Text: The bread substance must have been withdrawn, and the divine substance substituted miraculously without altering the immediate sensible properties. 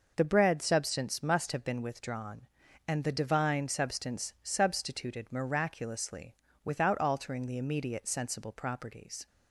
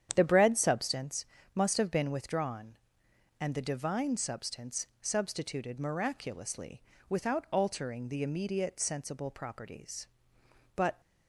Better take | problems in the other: first | starts louder than the rest; strong; until 1.1 s; 9 dB // pauses between "substance" and "must"; slight; at 1.2 s; 0.30 s long // pauses between "miraculously" and "without"; slight; at 6.8 s; 0.28 s long; slight in the first // goes on to say "But"; slight; from 10.7 s on; 0.24 s long

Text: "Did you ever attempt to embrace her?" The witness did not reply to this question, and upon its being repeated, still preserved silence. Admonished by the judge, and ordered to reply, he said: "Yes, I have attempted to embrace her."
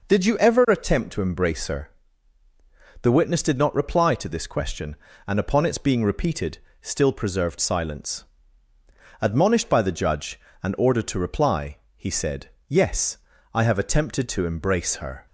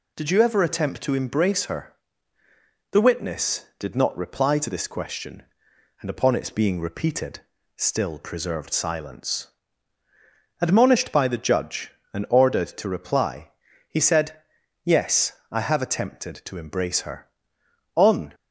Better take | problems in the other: first | goes on to say "On"; slight; from 17.9 s on; 0.40 s long

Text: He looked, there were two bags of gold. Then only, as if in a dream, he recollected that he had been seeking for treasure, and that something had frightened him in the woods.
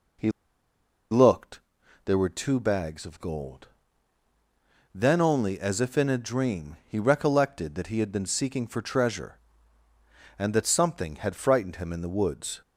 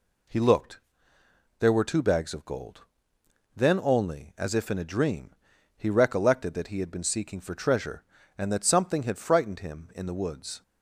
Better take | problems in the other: second | pauses between "He" and "looked"; noticeable; at 0.2 s; 0.81 s long

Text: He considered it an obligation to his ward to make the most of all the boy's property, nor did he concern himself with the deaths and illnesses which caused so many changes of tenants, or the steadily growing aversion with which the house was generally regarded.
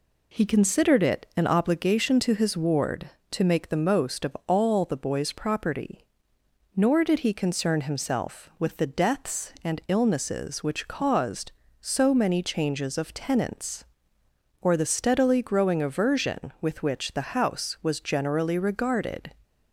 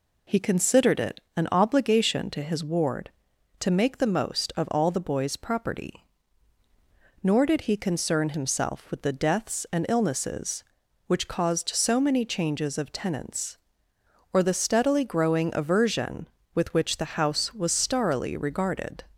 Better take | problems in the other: first | pauses between "it" and "an"; slight; at 1.2 s; 0.16 s long // says "starrily" for "generally"; at 17.7 s

